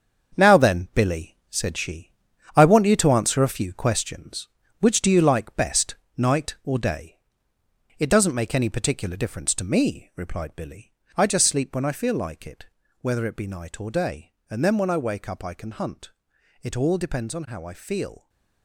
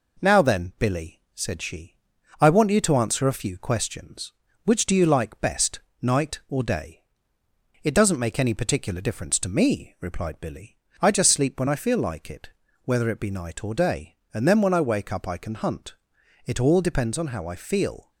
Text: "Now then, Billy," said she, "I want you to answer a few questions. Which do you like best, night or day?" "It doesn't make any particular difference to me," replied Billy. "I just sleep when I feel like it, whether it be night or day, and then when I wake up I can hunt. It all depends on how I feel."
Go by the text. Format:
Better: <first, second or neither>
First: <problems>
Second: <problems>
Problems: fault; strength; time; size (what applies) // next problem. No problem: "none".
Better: second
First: gets quieter; strong; throughout; 9 dB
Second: none